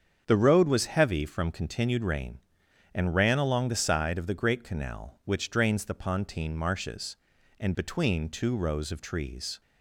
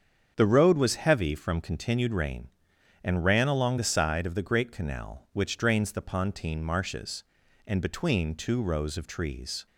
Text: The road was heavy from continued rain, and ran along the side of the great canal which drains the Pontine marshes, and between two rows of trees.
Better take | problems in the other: neither | starts louder than the rest; strong; the same in both

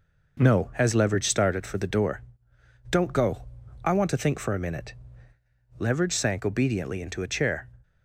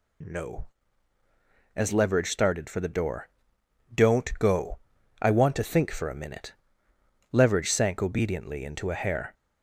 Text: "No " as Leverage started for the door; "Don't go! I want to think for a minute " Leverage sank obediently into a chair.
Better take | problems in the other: first | says "hair" for "chair"; at 8.9 s

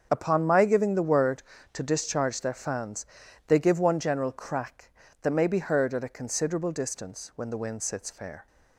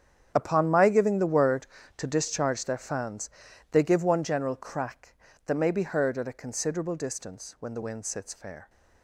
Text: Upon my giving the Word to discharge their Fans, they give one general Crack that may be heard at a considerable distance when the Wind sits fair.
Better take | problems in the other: first | gets quieter; strong; throughout; 15 dB // starts louder than the rest; strong; until 1.3 s; 8.5 dB; also in the first

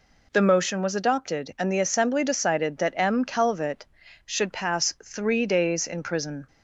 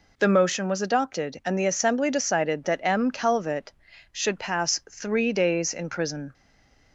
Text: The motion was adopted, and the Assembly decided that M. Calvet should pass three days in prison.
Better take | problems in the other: first | stays silent after the last word; slight; from 6.3 s on; 0.6 s long

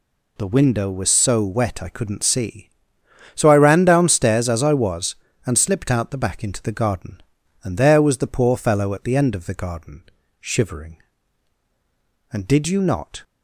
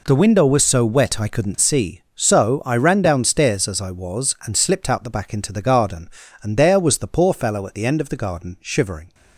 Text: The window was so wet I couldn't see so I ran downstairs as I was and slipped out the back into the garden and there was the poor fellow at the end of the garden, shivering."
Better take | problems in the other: second | goes on to say "And did you not"; noticeable; from 12.3 s on; 0.90 s long

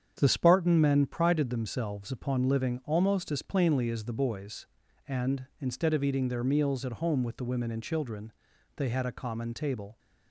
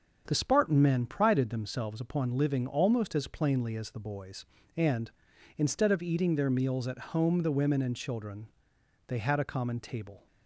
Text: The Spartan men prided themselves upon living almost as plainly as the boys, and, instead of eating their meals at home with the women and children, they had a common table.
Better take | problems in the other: first | starts louder than the rest; until 1.2 s; 6.5 dB; strong in the first // skips "with"; at 7.4 s

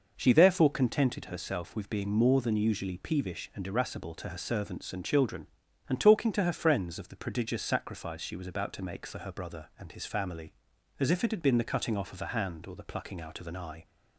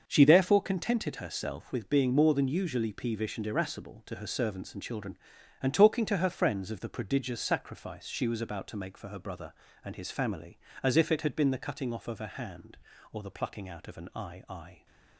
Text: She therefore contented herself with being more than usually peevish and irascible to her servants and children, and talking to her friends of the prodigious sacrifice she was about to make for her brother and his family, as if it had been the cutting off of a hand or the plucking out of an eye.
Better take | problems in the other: first | starts louder than the rest; until 1.0 s; 6.5 dB // says "eye" twice; at 14.4 s

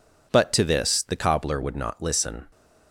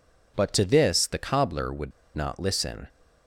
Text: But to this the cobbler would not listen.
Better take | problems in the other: first | pauses between "would" and "not"; slight; at 1.9 s; 0.25 s long

